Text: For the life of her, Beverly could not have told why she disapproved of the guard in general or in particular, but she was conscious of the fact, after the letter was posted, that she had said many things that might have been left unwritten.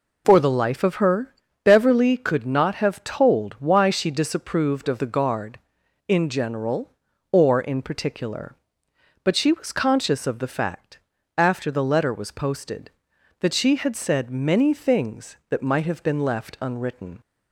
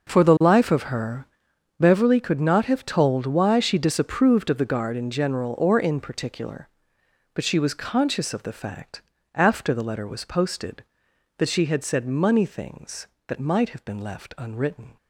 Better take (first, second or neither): first